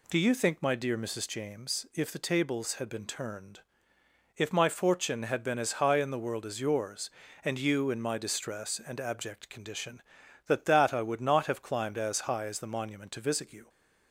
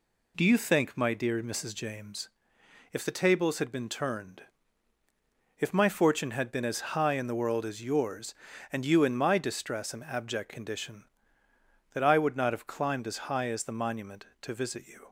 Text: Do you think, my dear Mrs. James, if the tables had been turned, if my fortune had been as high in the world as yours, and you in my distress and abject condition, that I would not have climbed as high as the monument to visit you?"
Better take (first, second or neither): second